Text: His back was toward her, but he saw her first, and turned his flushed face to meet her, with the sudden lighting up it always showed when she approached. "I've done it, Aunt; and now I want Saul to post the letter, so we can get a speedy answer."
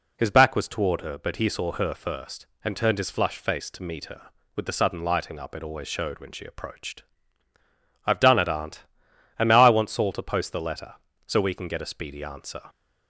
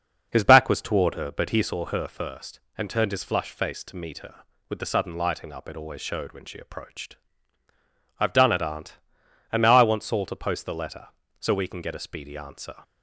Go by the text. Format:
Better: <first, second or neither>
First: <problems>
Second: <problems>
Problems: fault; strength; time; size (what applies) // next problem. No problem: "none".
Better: first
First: none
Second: starts louder than the rest; noticeable; until 1.7 s; 6 dB